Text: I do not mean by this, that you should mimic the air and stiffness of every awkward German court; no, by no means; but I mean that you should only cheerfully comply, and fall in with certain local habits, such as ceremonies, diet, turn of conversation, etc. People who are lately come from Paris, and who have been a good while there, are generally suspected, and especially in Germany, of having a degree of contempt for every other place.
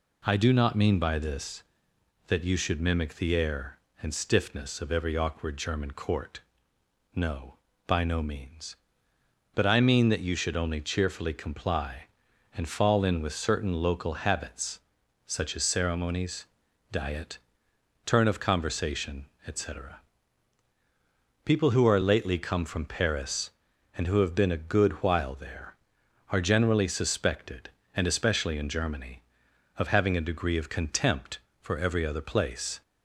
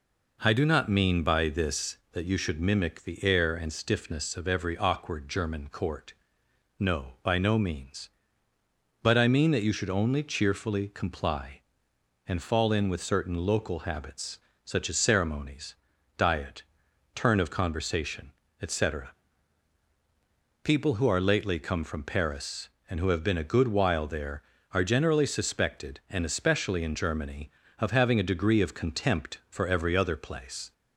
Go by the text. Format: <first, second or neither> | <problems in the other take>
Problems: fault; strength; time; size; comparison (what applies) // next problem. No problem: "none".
neither | none